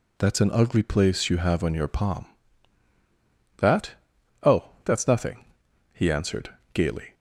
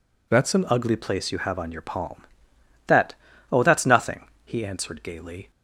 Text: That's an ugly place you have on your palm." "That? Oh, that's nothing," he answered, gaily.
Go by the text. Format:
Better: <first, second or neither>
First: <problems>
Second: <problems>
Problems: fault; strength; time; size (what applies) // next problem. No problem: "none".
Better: first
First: none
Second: changes voice at "ugly"; from 0.6 s on; 4.9 s long